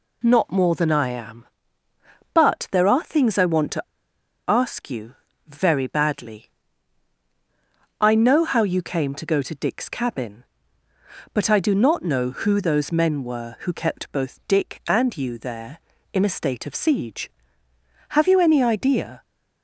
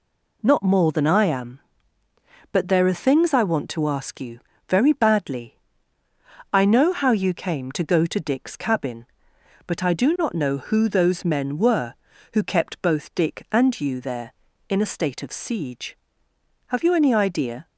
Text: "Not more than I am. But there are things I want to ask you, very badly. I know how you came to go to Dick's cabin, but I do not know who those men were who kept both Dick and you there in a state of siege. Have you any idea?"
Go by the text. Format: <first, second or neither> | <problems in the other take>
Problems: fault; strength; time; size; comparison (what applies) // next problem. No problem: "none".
second | pauses between "to" and "ask"; noticeable; at 3.8 s; 0.66 s long